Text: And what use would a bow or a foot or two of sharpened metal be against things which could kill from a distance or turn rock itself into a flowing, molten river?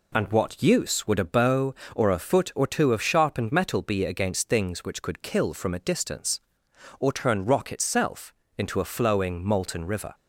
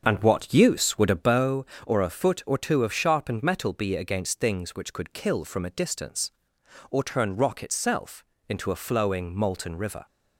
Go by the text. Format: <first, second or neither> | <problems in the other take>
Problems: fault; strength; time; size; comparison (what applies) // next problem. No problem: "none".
first | starts louder than the rest; until 1.5 s; 6.5 dB // pauses between "itself" and "into"; slight; at 8.2 s; 0.24 s long; slight in the first